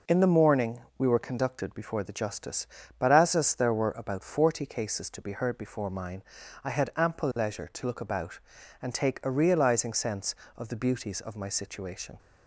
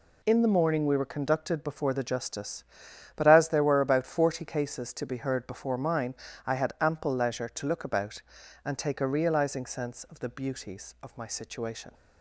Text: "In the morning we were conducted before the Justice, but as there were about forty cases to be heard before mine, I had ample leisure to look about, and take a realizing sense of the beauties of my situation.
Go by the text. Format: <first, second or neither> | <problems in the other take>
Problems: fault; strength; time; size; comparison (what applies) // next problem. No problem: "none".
second | pauses between "morning" and "we"; slight; at 0.8 s; 0.16 s long // says "as" twice; at 3.3 s